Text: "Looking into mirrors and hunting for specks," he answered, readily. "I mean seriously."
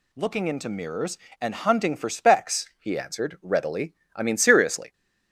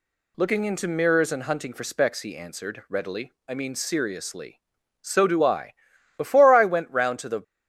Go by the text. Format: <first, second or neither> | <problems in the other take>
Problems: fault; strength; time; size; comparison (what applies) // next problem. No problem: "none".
first | goes on to say "So do I Before I went round to the"; strong; from 5.0 s on; 2.4 s long